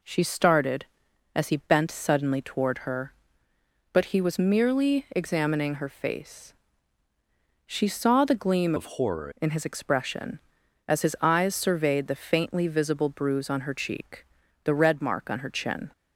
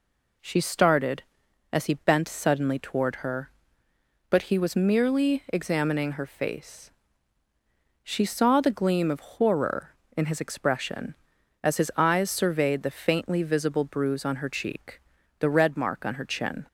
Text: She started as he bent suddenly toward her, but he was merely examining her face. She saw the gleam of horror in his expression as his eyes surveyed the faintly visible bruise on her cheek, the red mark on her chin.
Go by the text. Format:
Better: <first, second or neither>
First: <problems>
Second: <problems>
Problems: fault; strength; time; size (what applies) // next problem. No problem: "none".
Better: second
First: changes voice from "of" to "horror"; from 8.7 to 9.3 s; 0.6 s long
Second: none